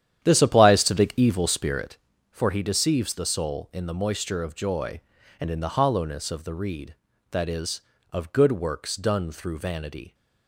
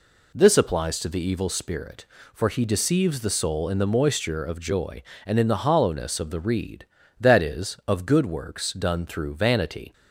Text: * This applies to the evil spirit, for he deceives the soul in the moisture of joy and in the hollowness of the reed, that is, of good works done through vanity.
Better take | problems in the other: second | starts louder than the rest; strong; until 1.9 s; 10 dB

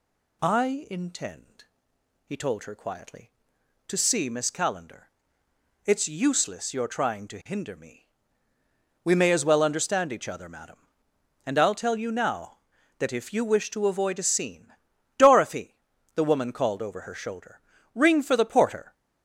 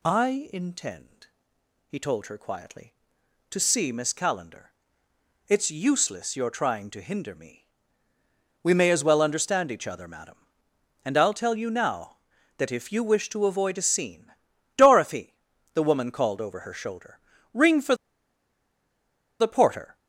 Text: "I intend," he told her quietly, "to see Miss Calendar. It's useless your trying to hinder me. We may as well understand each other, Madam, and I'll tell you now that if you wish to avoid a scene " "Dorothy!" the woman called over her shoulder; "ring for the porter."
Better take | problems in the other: first | pauses between "for" and "the"; strong; at 17.9 s; 1.4 s long

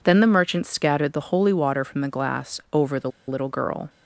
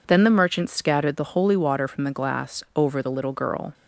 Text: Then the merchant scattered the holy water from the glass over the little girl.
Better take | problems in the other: second | pauses between "the" and "little"; slight; at 3.1 s; 0.17 s long

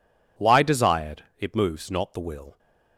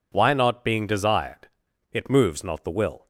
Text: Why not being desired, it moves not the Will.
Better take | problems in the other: second | skips "not being"; at 0.6 s

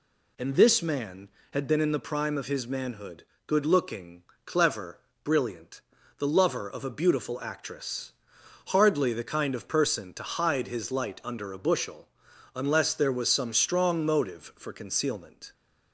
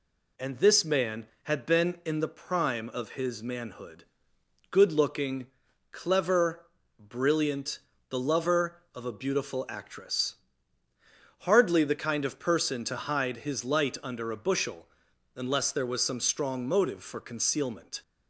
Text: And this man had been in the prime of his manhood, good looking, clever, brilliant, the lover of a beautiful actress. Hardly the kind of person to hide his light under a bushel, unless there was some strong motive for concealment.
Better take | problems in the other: neither | none

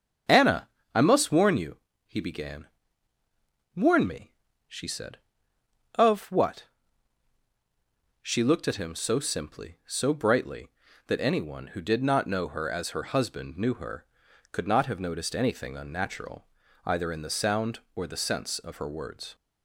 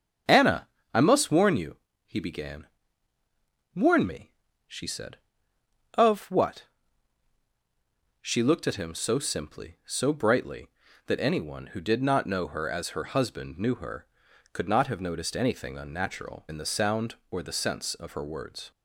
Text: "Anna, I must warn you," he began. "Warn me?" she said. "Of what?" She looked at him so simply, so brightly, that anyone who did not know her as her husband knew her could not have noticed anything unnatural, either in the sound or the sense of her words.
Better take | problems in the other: first | starts louder than the rest; strong; until 1.5 s; 7.5 dB; strong in the first // skips "either"; at 16.4 s

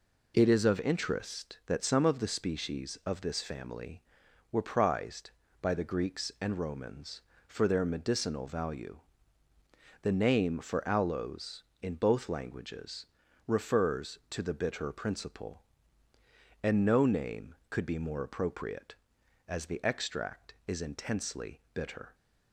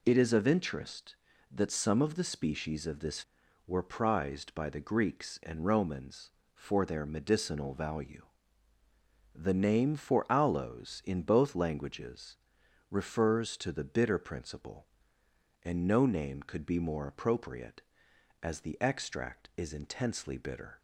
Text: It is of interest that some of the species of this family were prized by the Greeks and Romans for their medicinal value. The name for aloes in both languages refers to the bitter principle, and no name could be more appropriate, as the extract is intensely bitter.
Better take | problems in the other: first | skips "family"; at 3.4 s // pauses between "languages" and "refers"; noticeable; at 12.3 s; 0.54 s long; also in the first

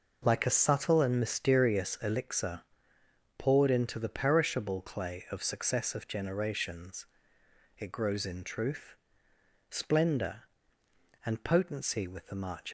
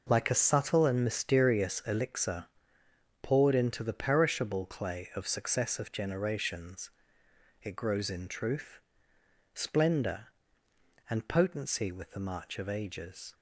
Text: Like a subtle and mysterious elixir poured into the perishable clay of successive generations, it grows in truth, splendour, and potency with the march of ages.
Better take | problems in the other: second | pauses between "elixir" and "poured"; noticeable; at 2.6 s; 0.76 s long; noticeable in the second // stops before "of ages"; at 12.6 s

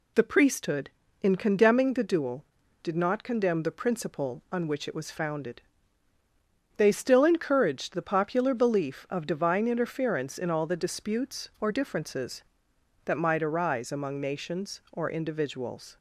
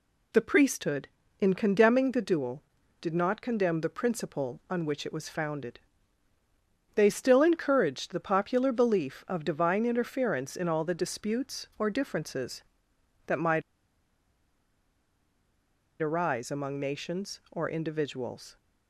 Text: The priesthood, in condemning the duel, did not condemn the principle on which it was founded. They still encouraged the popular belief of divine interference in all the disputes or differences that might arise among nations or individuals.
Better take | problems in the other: first | pauses between "might" and "arise"; strong; at 13.6 s; 2.4 s long

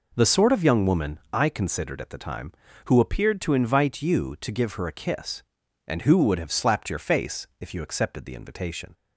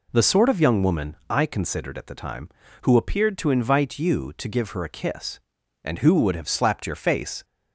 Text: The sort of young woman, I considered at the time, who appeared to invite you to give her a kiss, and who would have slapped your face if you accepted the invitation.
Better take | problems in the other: first | stops before "if you accepted the invitation"; at 7.4 s

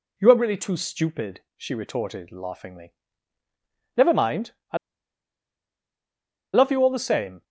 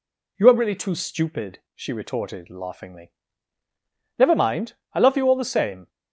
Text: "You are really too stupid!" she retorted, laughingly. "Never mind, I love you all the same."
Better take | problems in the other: second | pauses between "I" and "love"; strong; at 4.7 s; 1.7 s long

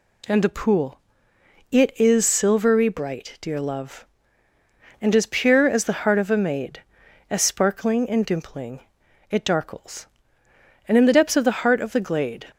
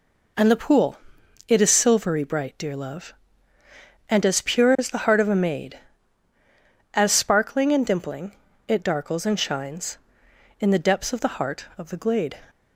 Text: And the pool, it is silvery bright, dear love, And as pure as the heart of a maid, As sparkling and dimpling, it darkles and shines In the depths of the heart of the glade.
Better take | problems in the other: second | skips "shines"; at 10.9 s

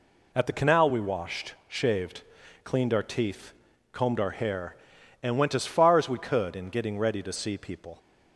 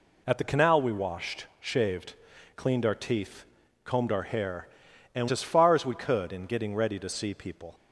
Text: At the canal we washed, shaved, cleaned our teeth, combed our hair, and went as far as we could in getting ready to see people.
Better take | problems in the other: first | skips "went"; at 5.2 s

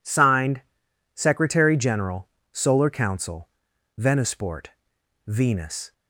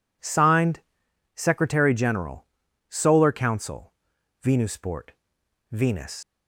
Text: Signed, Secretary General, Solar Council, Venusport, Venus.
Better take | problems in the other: first | leaves "Venus" unfinished; at 6.2 s; 90 ms

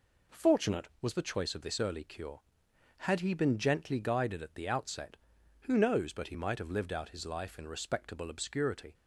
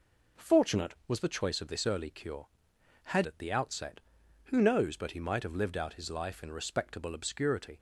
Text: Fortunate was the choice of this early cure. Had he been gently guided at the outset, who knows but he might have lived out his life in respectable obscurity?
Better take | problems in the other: first | skips "he been gently guided"; at 3.2 s

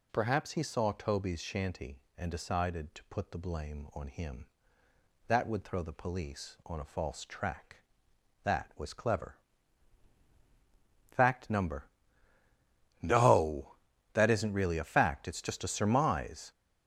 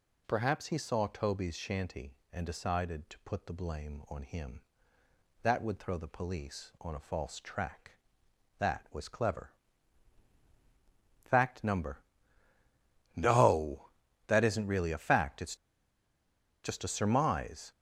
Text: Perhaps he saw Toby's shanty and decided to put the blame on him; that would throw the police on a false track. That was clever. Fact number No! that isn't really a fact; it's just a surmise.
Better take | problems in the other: first | pauses between "number" and "No"; at 11.9 s; 1.1 s long; also in the first // pauses between "it's" and "just"; at 15.5 s; 1.0 s long

